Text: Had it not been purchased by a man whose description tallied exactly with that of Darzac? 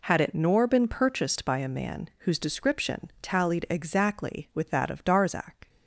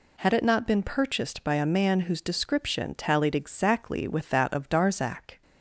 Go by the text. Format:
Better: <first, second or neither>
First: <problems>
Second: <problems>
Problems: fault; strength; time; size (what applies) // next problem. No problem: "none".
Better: second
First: says "nor" for "not"; at 0.3 s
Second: none